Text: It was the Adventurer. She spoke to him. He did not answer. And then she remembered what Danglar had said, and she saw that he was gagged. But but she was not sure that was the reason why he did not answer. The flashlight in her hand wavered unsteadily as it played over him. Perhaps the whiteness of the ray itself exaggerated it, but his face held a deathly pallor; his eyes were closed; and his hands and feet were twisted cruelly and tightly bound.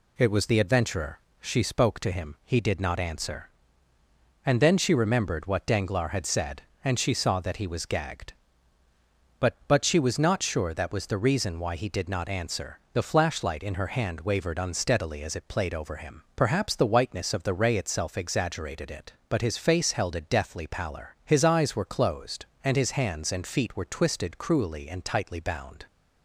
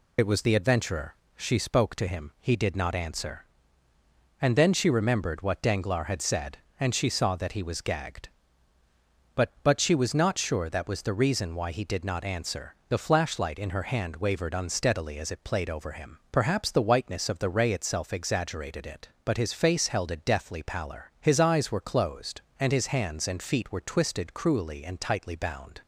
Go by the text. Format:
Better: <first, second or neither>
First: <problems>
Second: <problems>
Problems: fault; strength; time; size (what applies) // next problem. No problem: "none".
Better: first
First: none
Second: loses the start of "It"; at 0.1 s; 50 ms